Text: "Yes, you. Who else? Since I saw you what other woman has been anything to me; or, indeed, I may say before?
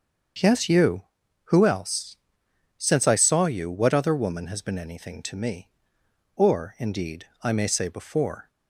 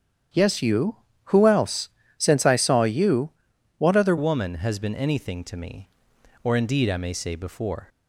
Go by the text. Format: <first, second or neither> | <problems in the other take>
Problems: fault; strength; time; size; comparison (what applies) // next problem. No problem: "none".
first | starts louder than the rest; strong; until 1.6 s; 9.5 dB; also in the first // pauses between "you" and "what"; noticeable; at 3.2 s; 0.48 s long // changes voice at "woman"; from 4.1 s on; 3.7 s long